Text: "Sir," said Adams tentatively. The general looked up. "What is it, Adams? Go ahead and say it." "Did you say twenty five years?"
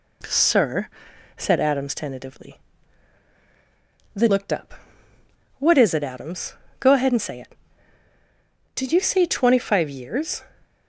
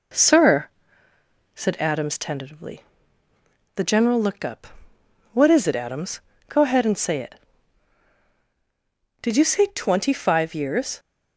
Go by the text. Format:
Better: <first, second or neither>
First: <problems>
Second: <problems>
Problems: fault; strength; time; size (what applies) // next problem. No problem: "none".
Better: second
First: skips "general"; at 4.2 s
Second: none